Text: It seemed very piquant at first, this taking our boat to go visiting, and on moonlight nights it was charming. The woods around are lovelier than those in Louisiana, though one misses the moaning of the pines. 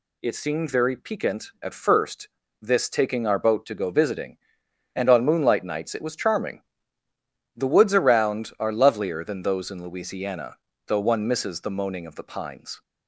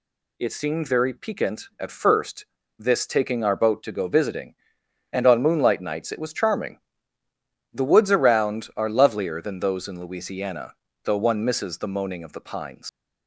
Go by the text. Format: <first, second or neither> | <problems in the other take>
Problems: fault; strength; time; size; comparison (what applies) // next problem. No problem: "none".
first | leaves "pines" unfinished; at 12.8 s; 90 ms